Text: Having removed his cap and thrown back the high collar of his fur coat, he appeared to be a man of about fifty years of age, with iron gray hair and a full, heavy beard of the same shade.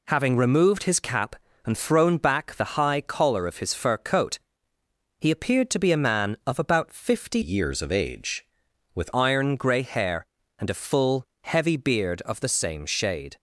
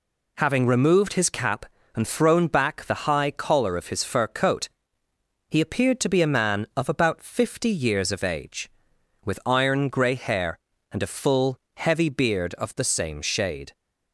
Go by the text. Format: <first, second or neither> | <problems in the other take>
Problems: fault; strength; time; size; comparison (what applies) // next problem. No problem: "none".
second | changes voice from "years" to "with"; from 7.4 to 9.0 s; 1.6 s long